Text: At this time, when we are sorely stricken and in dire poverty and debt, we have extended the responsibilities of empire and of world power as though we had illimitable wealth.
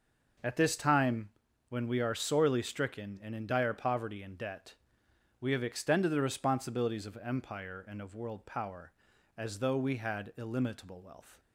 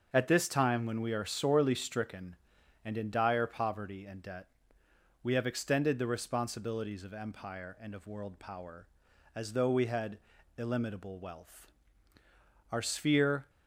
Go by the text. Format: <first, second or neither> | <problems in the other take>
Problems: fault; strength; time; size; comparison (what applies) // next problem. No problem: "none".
first | starts louder than the rest; until 1.1 s; 6.5 dB // pauses between "had" and "illimitable"; at 10.1 s; 0.40 s long // goes on to say "Our sphere"; noticeable; from 12.7 s on; 0.78 s long